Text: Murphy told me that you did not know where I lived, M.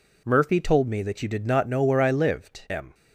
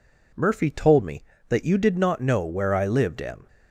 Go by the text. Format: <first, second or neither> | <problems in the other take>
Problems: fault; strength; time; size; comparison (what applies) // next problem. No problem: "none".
neither | none